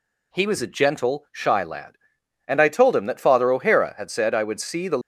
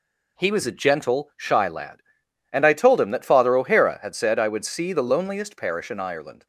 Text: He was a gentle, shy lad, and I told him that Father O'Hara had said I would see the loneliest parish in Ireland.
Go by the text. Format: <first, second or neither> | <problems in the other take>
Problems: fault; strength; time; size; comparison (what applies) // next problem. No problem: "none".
second | stops before "loneliest parish in Ireland"; at 5.0 s